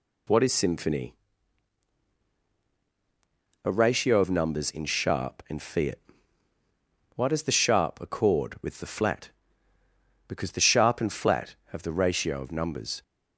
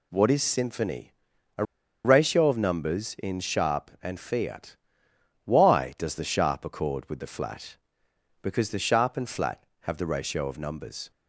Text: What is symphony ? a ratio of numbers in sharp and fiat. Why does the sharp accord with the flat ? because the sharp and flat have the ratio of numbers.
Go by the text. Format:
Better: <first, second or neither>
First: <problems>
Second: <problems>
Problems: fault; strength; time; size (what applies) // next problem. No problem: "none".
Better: first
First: none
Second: pauses between "a" and "ratio"; at 1.6 s; 0.41 s long